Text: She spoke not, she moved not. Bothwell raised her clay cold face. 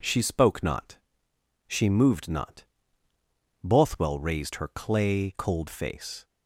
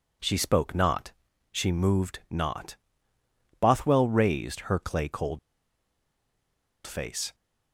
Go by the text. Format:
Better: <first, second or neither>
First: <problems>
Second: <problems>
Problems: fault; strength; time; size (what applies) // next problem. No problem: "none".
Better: first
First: none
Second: pauses between "cold" and "face"; strong; at 5.3 s; 1.4 s long